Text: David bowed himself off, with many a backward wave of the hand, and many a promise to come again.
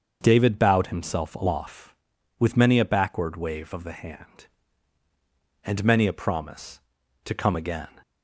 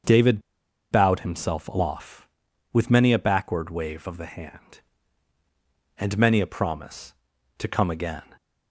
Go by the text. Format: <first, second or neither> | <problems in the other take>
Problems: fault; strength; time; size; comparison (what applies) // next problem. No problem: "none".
first | starts louder than the rest; until 1.5 s; 6.5 dB; also in the first // pauses between "David" and "bowed"; noticeable; at 0.3 s; 0.52 s long